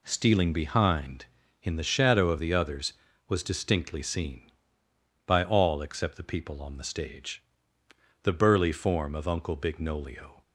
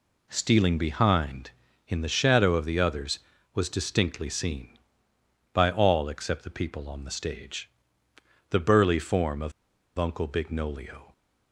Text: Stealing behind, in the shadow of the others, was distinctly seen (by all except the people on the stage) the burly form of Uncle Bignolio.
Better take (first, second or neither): first